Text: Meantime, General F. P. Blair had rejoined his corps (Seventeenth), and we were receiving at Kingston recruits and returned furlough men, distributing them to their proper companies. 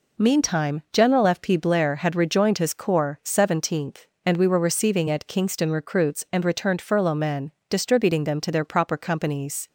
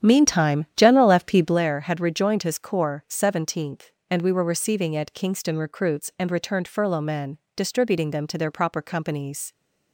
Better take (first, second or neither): first